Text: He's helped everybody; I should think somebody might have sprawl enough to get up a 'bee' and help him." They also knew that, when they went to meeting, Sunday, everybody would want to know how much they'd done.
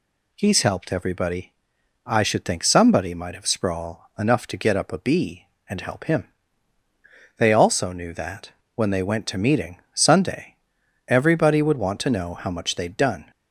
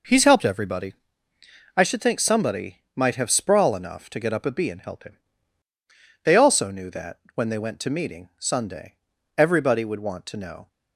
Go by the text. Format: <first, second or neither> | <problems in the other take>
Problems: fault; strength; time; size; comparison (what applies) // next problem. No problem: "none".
first | stops before "how much they'd done"; at 10.6 s